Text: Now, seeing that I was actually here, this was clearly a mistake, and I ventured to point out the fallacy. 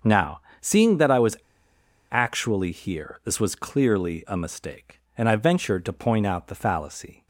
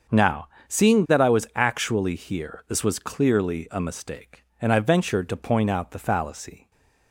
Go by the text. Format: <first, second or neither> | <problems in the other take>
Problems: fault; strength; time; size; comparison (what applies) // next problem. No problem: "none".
second | starts louder than the rest; until 1.2 s; 6.5 dB; also in the second // pauses between "was" and "actually"; noticeable; at 1.3 s; 0.74 s long